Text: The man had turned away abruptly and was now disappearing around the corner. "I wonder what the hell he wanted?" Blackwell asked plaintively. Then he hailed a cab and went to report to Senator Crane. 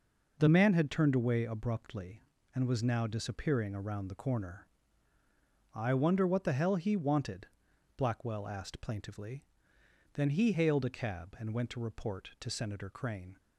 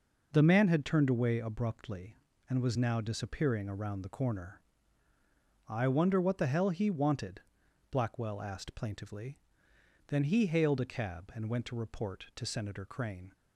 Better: neither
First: none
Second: none

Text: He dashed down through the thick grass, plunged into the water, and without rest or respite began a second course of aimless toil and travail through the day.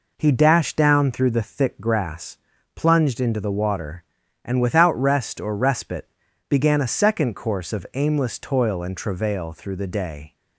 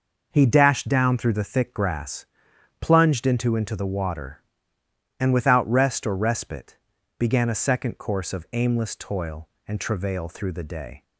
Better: first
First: pauses between "respite" and "began"; at 6.0 s; 0.42 s long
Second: says "into" twice; at 3.5 s // pauses between "respite" and "began"; at 6.7 s; 0.42 s long

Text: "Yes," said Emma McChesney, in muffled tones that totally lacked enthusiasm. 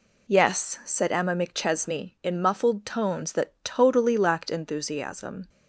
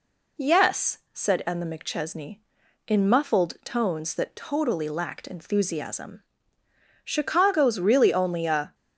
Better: first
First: none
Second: goes on to say "Chicago's really only a"; from 7.2 s on; 1.5 s long

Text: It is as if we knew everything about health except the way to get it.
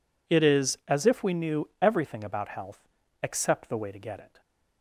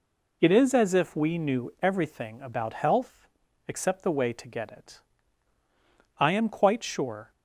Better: first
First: pauses between "health" and "except"; slight; at 2.8 s; 0.34 s long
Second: pauses between "health" and "except"; at 3.2 s; 0.42 s long // goes on to say "I am quite sure"; noticeable; from 6.1 s on; 1.1 s long

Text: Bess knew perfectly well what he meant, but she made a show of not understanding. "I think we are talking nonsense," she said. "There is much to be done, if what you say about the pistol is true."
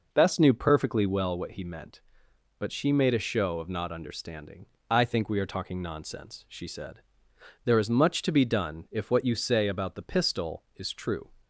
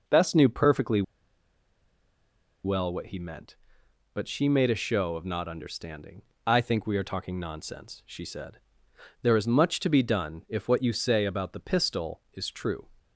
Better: first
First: none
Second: pauses between "perfectly" and "well"; strong; at 1.0 s; 1.6 s long

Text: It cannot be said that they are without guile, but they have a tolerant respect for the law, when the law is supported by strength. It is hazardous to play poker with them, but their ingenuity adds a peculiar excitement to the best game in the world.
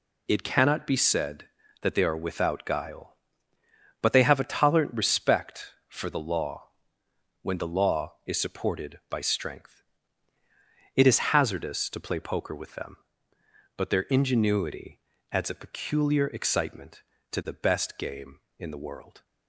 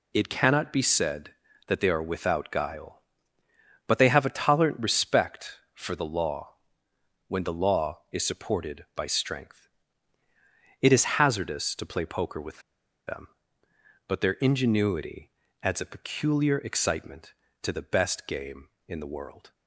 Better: first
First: pauses between "ingenuity" and "adds"; slight; at 15.0 s; 0.32 s long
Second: pauses between "with" and "them"; noticeable; at 12.6 s; 0.47 s long // pauses between "ingenuity" and "adds"; slight; at 15.3 s; 0.32 s long

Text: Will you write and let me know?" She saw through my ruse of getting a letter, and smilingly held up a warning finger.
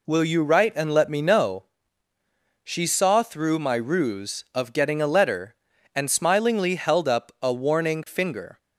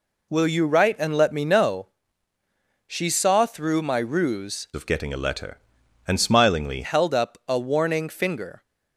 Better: first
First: none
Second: changes voice from "of" to "smilingly"; from 4.7 to 6.8 s; 2.1 s long

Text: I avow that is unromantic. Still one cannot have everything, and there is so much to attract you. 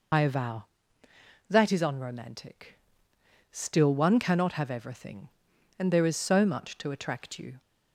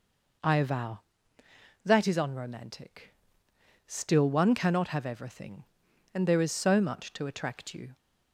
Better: second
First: loses the start of "I"; at 0.1 s; 60 ms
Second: none

